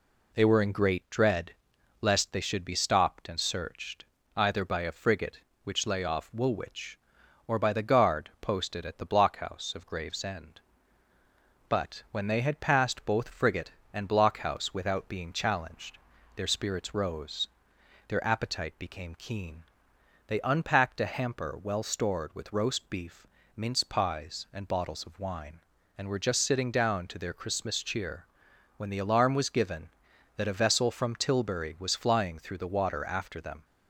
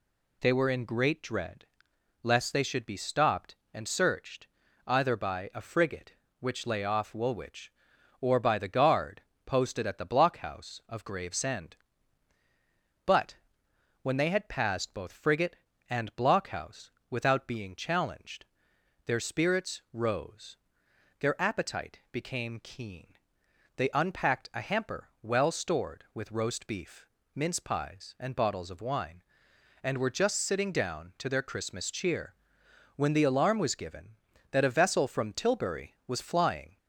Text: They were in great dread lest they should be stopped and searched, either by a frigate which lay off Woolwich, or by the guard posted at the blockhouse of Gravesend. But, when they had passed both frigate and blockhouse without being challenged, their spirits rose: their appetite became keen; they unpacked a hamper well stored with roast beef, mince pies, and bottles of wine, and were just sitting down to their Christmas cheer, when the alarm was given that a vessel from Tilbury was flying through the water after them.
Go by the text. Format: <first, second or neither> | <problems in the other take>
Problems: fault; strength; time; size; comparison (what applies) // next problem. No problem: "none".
first | pauses between "dread" and "lest"; noticeable; at 1.6 s; 0.58 s long; noticeable in the first // pauses between "guard" and "posted"; slight; at 9.2 s; 0.24 s long // pauses between "blockhouse" and "without"; slight; at 16.8 s; 0.20 s long // stops before "through the water after them"; at 36.7 s